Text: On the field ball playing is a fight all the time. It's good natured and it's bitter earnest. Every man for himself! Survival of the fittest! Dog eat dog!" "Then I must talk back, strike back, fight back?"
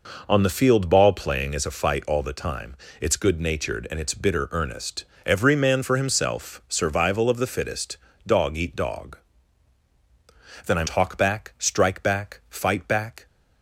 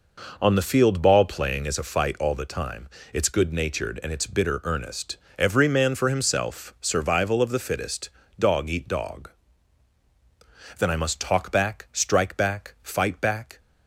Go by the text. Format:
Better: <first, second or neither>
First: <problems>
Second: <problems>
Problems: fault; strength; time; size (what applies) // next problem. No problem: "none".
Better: second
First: skips "must"; at 10.8 s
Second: none